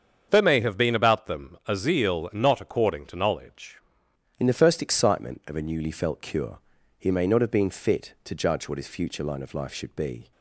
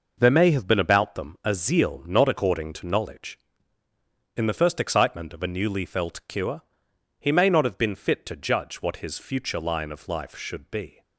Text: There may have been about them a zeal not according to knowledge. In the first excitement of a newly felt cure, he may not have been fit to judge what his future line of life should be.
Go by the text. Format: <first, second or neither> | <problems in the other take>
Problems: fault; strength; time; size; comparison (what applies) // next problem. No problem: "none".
second | starts louder than the rest; strong; until 1.3 s; 7 dB // changes voice at "In"; from 4.3 s on; 6.0 s long